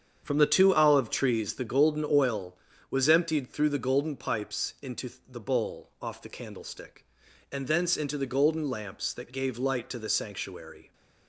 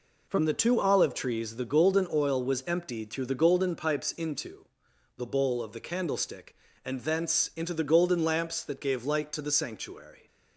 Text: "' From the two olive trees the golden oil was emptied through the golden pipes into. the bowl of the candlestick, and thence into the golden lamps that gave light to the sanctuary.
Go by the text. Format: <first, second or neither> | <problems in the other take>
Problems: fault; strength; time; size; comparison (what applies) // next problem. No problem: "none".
second | starts louder than the rest; strong; until 1.2 s; 7.5 dB // says "off" for "of"; at 6.0 s